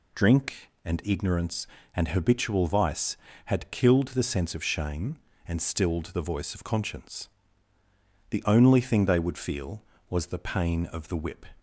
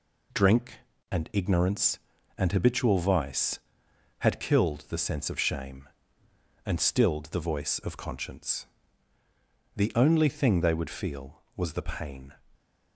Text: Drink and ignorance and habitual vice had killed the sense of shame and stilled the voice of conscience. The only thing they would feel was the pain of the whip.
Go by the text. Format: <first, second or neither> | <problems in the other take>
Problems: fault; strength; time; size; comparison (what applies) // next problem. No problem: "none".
first | stops before "of the whip"; at 12.5 s